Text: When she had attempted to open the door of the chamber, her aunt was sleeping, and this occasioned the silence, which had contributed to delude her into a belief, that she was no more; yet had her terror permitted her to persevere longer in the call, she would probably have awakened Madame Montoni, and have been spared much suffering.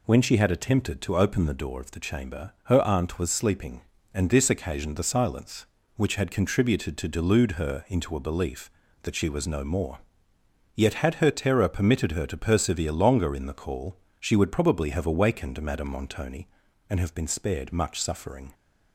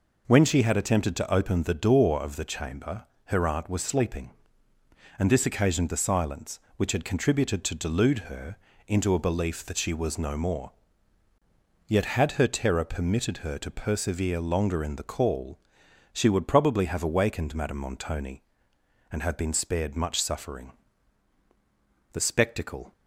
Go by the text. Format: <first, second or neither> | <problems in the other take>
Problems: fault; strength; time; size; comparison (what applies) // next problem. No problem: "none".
first | pauses between "her" and "into"; slight; at 8.5 s; 0.32 s long // goes on to say "The spectacle"; noticeable; from 22.1 s on; 0.78 s long